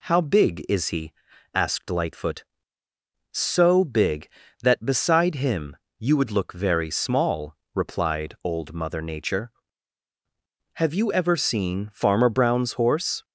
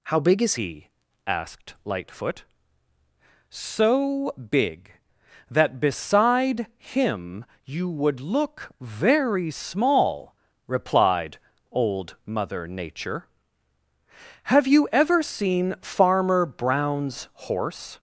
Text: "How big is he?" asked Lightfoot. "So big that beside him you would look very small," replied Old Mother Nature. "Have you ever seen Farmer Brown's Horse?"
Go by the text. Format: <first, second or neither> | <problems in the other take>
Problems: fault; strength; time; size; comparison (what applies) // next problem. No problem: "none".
first | changes voice at "he"; from 0.5 s on; 17.4 s long // pauses between "him" and "you"; slight; at 7.4 s; 0.18 s long; slight in the first // pauses between "replied" and "Old"; slight; at 11.3 s; 0.34 s long // pauses between "Brown's" and "Horse"; slight; at 17.2 s; 0.18 s long